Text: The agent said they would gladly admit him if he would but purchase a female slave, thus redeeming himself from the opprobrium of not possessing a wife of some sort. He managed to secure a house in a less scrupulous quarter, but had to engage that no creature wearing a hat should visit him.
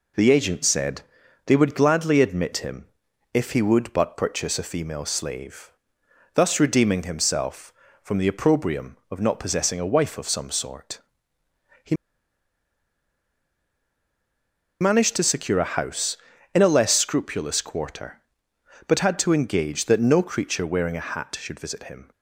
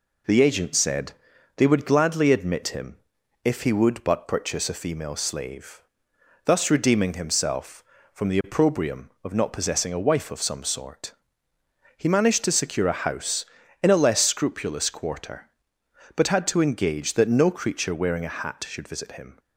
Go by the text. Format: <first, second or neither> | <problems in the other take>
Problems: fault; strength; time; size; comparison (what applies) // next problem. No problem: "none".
second | pauses between "said" and "they"; noticeable; at 1.0 s; 0.46 s long; noticeable in the second // pauses between "him" and "if"; noticeable; at 2.8 s; 0.46 s long; noticeable in the second // pauses between "He" and "managed"; strong; at 11.9 s; 2.8 s long